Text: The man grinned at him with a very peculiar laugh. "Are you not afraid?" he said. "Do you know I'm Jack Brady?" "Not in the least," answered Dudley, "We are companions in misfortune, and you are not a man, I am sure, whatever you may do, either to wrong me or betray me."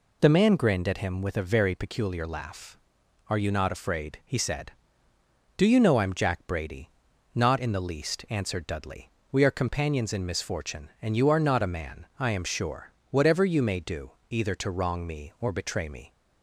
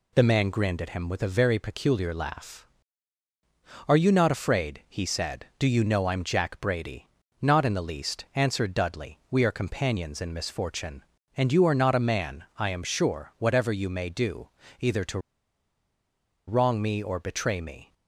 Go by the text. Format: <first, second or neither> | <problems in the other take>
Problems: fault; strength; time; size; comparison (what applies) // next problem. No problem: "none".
first | pauses between "to" and "wrong"; strong; at 15.1 s; 1.2 s long